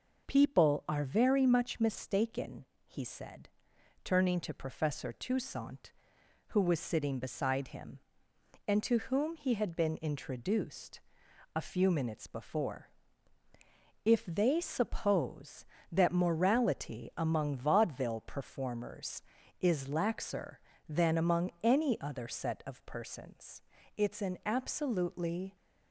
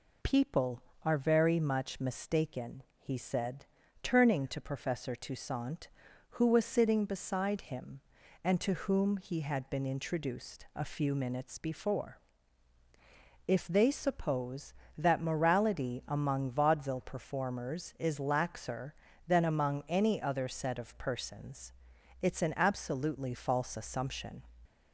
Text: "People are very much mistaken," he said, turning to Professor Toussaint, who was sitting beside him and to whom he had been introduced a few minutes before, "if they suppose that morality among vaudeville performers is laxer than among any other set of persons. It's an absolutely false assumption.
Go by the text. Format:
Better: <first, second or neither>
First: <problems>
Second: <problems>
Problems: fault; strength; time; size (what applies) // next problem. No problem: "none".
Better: second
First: pauses between "introduced" and "a"; noticeable; at 10.9 s; 0.56 s long // stops before "false assumption"; at 25.5 s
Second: none